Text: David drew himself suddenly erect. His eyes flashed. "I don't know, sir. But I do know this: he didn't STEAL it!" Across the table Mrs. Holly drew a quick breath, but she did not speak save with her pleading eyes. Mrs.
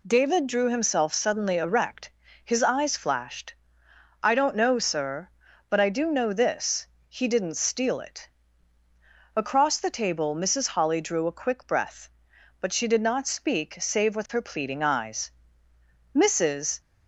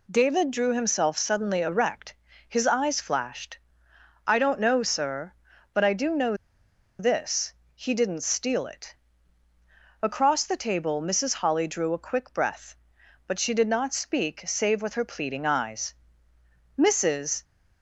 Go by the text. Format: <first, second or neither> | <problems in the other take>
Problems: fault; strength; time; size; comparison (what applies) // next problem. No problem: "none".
first | pauses between "know" and "this"; noticeable; at 6.3 s; 0.64 s long